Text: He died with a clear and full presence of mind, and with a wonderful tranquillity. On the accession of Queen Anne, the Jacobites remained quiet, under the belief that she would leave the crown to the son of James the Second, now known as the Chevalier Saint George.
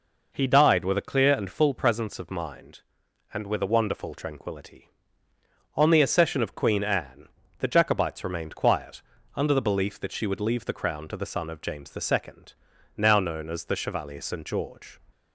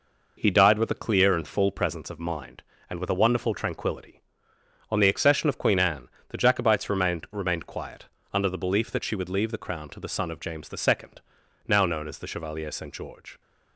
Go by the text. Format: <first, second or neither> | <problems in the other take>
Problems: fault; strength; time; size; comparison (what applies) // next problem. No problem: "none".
first | says "remained" twice; at 7.3 s